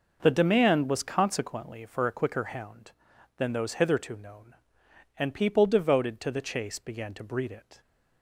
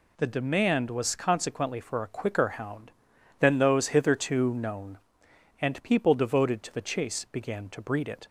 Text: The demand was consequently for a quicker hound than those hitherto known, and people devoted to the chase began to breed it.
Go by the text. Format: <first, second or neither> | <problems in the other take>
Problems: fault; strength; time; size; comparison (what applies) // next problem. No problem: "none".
neither | none